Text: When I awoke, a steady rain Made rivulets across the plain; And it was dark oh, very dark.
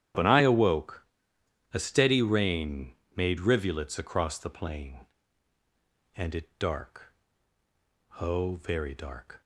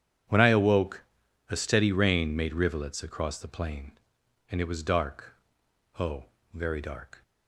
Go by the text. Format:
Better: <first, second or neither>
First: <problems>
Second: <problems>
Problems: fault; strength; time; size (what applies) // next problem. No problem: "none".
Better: second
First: starts louder than the rest; strong; until 1.8 s; 10.5 dB // pauses between "rain" and "Made"; slight; at 2.9 s; 0.24 s long // skips "was"; at 6.5 s // pauses between "dark" and "oh"; at 7.1 s; 1.0 s long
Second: pauses between "dark" and "oh"; noticeable; at 5.3 s; 0.64 s long